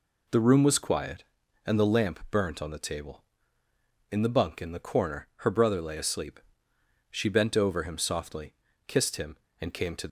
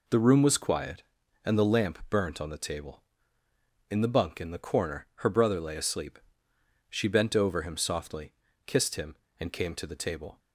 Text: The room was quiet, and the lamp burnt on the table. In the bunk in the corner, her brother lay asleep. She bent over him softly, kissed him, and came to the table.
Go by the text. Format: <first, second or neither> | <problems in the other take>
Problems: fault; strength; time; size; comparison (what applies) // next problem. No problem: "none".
second | stops before "the table"; at 10.0 s